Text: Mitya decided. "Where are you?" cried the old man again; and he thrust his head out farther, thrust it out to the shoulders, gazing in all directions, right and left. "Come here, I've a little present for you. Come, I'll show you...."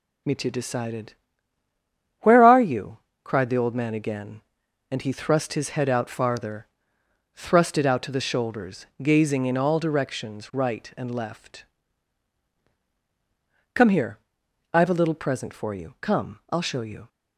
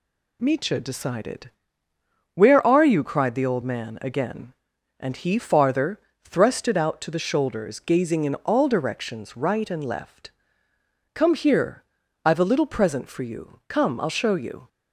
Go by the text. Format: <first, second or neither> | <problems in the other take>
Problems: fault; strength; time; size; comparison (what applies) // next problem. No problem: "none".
first | skips "thrust his head out"; at 5.3 s